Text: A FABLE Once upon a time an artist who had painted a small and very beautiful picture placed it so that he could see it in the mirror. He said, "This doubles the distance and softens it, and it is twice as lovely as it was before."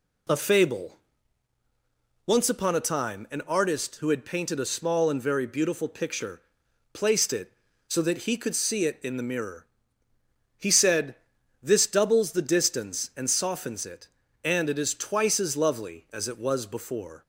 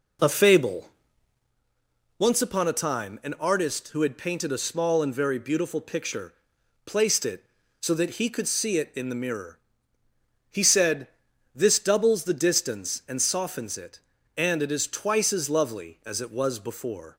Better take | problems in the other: first | starts louder than the rest; until 1.5 s; 3.5 dB // pauses between "FABLE" and "Once"; strong; at 0.9 s; 1.2 s long; strong in the first // pauses between "picture" and "placed"; noticeable; at 6.3 s; 0.50 s long; noticeable in the first

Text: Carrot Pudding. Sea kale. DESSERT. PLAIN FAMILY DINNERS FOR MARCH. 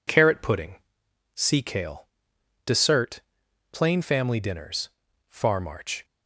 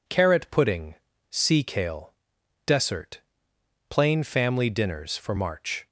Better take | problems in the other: second | says "Far" for "FOR"; at 5.2 s

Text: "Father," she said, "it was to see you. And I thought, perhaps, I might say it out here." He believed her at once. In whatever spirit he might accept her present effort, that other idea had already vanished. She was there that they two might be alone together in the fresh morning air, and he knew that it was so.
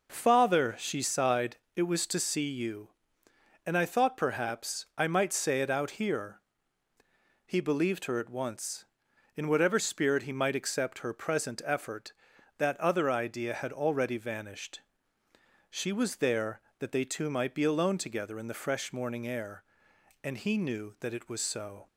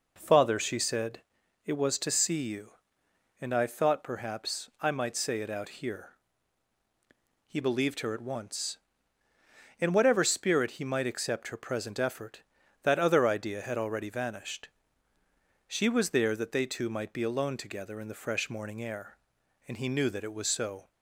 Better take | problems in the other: second | says "sighed" for "said"; at 1.0 s

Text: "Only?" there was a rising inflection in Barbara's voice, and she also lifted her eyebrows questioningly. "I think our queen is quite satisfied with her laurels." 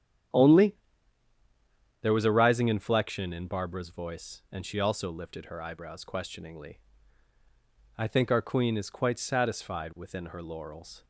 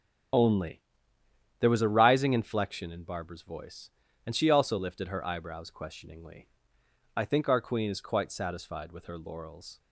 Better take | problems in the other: second | starts louder than the rest; strong; until 2.5 s; 9.5 dB; strong in the second // says "within" for "with"; at 9.9 s

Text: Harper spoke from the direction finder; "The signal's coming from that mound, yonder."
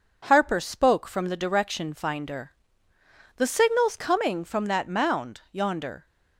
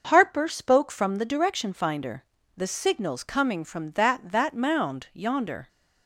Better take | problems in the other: first | starts louder than the rest; noticeable; until 1.1 s; 6 dB // says "that" twice; at 4.2 s

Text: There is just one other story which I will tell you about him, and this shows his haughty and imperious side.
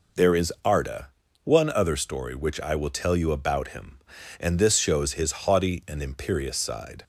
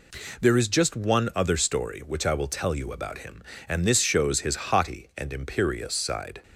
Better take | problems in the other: second | says "arda" for "just"; at 0.6 s

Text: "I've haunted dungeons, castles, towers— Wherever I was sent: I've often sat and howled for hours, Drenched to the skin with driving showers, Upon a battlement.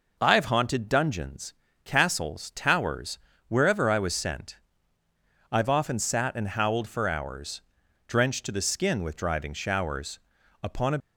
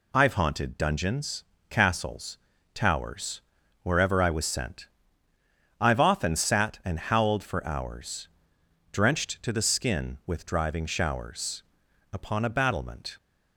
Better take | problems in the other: second | stops before "battlement"; at 10.9 s

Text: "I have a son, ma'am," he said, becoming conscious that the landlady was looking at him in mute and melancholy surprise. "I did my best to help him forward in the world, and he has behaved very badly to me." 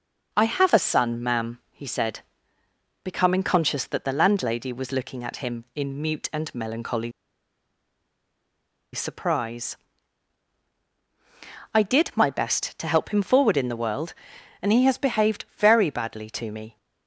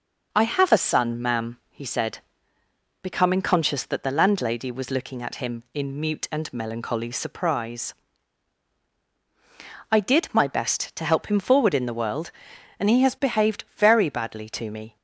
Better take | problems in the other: second | pauses between "melancholy" and "surprise"; strong; at 7.1 s; 1.8 s long

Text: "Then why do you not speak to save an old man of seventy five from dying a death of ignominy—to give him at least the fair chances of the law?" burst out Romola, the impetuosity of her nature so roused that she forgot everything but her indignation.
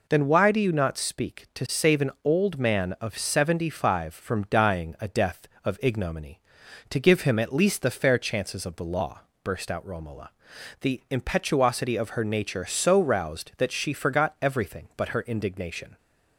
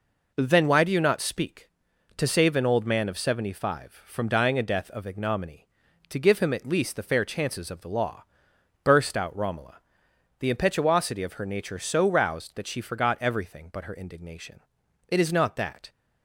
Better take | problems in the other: first | goes on to say "It is not that"; noticeable; from 15.0 s on; 0.82 s long

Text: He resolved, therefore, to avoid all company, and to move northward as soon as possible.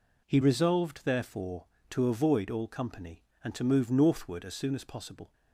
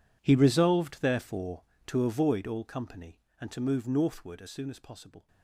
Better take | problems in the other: first | gets quieter; strong; throughout; 19 dB

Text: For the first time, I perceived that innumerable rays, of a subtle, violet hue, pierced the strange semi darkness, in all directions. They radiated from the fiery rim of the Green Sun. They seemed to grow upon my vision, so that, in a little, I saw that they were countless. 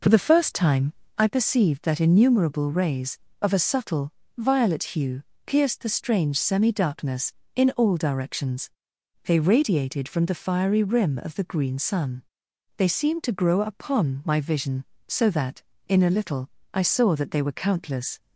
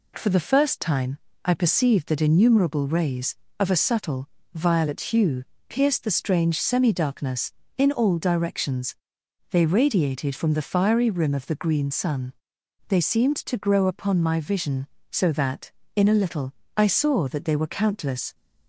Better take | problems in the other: second | starts louder than the rest; noticeable; until 1.2 s; 5 dB

